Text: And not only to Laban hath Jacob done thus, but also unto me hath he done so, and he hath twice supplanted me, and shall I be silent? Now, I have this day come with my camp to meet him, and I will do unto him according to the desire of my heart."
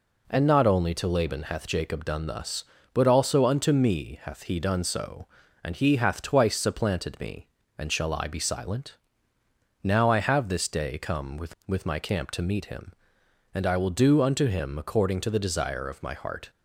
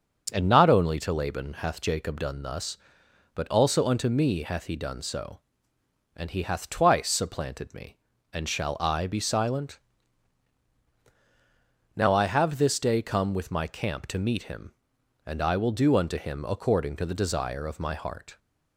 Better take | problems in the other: second | says "with" twice; at 11.6 s

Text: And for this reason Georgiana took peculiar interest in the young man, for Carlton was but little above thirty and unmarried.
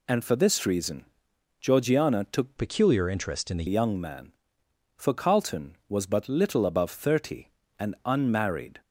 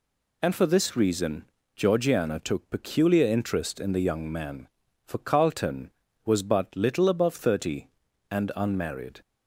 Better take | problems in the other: second | pauses between "reason" and "Georgiana"; noticeable; at 1.0 s; 0.54 s long; slight in the second // changes voice from "peculiar" to "the"; from 2.5 to 3.6 s; 1.1 s long

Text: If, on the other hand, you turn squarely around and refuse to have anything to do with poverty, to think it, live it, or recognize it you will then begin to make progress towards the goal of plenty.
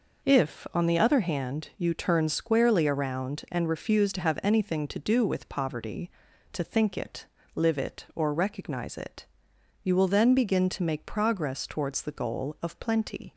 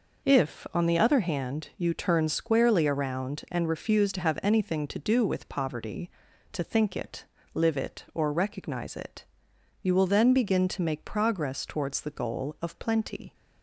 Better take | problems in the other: neither | pauses between "it" and "you"; noticeable; the same in both

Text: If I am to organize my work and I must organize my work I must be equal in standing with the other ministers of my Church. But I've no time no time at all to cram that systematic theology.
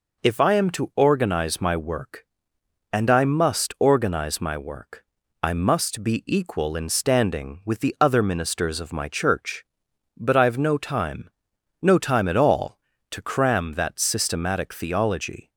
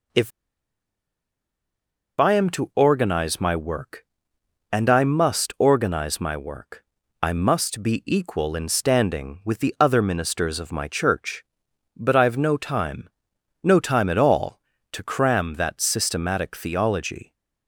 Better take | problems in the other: first | pauses between "If" and "I"; strong; at 0.3 s; 1.8 s long // pauses between "work" and "I"; at 6.8 s; 0.40 s long; also in the first // pauses between "time" and "no"; noticeable; at 13.0 s; 0.54 s long; noticeable in the first

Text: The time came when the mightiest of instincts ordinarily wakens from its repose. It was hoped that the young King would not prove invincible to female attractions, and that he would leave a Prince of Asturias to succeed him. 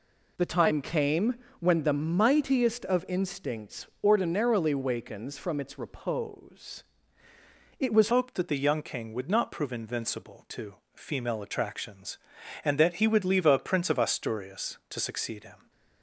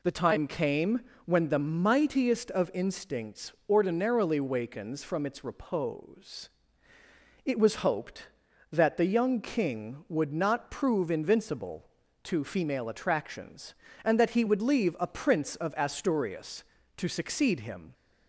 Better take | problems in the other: second | pauses between "came" and "when"; slight; at 1.3 s; 0.24 s long; slight in the second // pauses between "instincts" and "ordinarily"; slight; at 3.8 s; 0.16 s long; slight in the second // changes voice at "hoped"; from 8.1 s on; 7.5 s long // pauses between "to" and "female"; slight; at 10.7 s; 0.20 s long

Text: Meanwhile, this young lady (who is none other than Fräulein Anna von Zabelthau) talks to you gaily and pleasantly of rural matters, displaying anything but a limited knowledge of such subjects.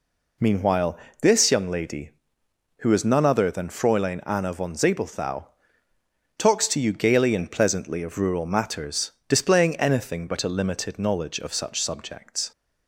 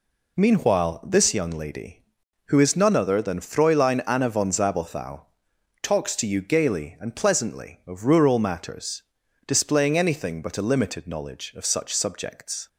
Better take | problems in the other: neither | none

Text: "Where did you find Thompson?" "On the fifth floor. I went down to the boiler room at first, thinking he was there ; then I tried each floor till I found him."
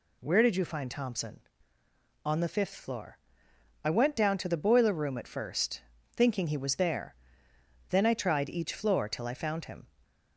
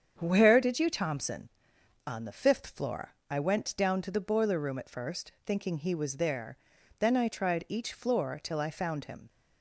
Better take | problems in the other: first | starts louder than the rest; strong; until 1.1 s; 8 dB // skips "find"; at 0.8 s

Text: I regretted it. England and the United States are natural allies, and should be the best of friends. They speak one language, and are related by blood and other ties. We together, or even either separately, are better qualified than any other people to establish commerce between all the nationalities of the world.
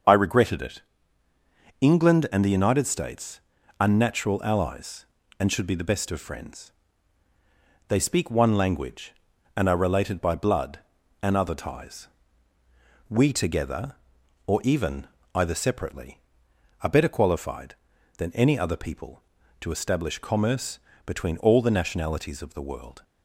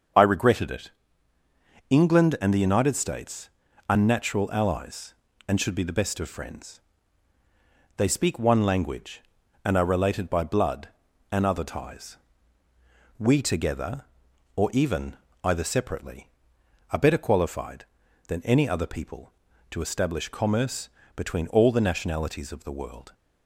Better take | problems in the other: neither | starts louder than the rest; the same in both // pauses between "even" and "either"; slight; the same in both // pauses between "commerce" and "between"; slight; the same in both

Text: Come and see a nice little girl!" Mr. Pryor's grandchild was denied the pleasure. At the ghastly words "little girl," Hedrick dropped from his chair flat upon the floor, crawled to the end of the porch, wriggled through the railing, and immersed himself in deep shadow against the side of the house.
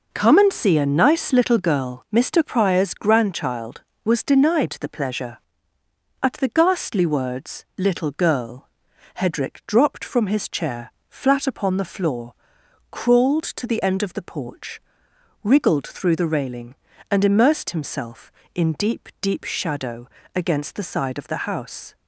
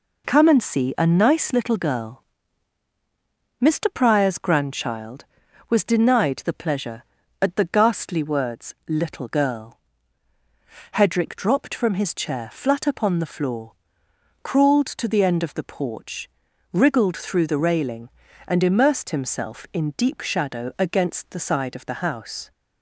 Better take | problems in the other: second | pauses between "chair" and "flat"; slight; at 10.9 s; 0.16 s long // says "deep" twice; at 19.2 s // pauses between "shadow" and "against"; slight; at 20.0 s; 0.28 s long

